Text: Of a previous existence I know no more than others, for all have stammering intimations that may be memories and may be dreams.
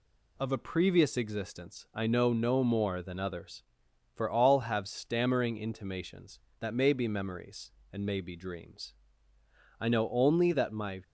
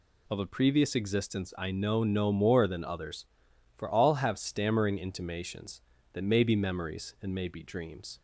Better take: second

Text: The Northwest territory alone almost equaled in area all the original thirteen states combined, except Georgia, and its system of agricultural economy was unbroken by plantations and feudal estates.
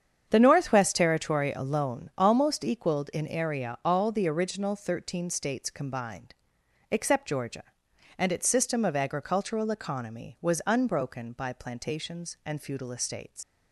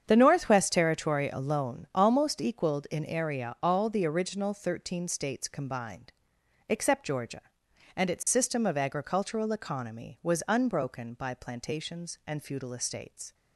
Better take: second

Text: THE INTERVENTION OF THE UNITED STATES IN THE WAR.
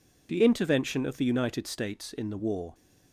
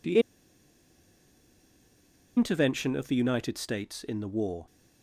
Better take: first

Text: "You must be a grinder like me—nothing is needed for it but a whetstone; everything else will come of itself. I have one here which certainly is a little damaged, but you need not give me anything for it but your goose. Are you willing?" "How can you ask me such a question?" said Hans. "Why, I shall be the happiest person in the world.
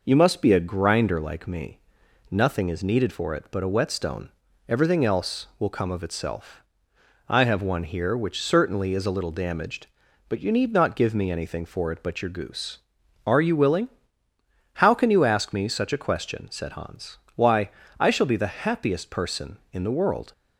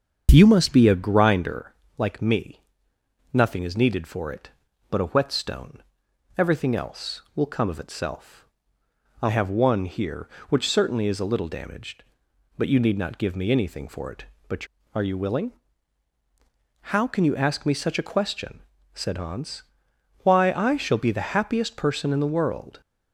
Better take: first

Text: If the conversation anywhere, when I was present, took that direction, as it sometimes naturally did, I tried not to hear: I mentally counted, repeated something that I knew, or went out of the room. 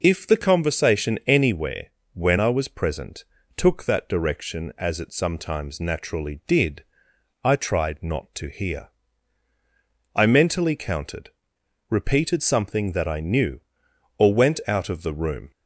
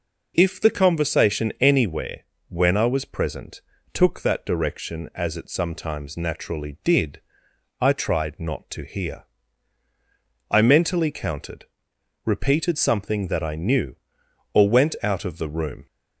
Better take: neither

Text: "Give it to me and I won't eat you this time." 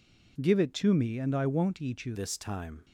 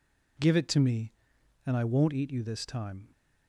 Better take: second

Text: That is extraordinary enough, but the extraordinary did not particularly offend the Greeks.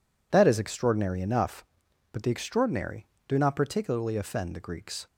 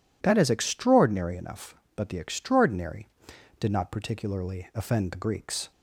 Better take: second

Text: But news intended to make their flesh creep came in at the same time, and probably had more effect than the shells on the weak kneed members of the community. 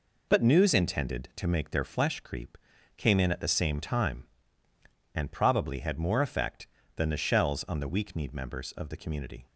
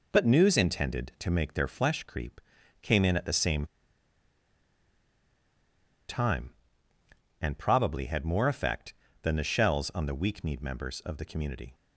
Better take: first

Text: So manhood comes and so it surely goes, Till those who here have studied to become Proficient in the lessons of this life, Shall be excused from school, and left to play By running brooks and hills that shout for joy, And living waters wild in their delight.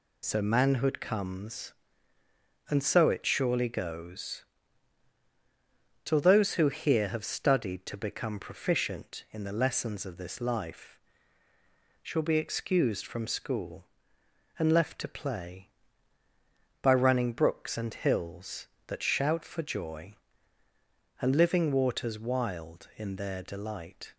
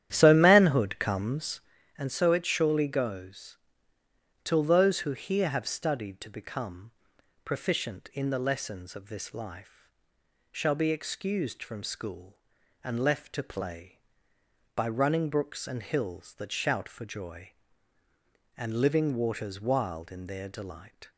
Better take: first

